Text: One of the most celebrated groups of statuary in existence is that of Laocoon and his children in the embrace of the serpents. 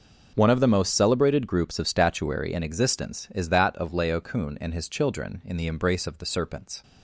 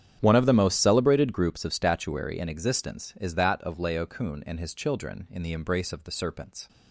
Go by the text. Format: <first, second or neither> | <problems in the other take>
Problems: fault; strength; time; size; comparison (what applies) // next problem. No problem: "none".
first | starts louder than the rest; strong; until 1.6 s; 9.5 dB